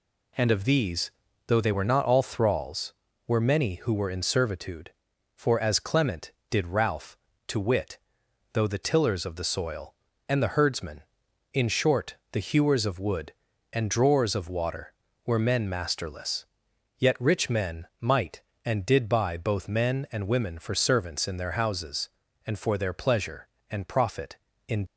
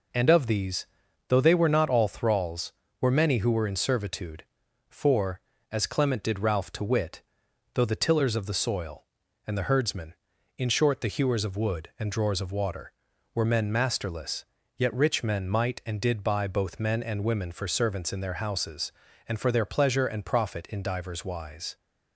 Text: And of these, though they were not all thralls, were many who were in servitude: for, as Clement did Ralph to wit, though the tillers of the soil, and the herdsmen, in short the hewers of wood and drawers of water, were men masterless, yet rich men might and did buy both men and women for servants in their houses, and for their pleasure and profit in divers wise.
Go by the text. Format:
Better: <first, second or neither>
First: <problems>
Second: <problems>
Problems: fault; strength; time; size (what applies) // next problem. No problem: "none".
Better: second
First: pauses between "short" and "the"; slight; at 12.1 s; 0.16 s long // stops before "divers wise"; at 24.8 s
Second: none